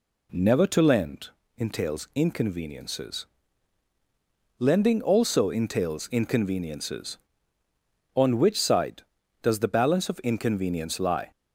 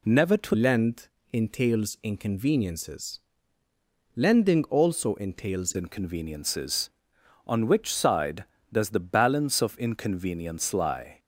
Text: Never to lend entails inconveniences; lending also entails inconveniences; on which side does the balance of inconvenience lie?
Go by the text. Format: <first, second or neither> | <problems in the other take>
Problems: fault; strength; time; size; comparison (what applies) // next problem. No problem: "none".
first | changes voice from "lend" to "entails"; from 0.5 to 5.7 s; 5.2 s long // pauses between "lend" and "entails"; slight; at 1.0 s; 0.24 s long; slight in the first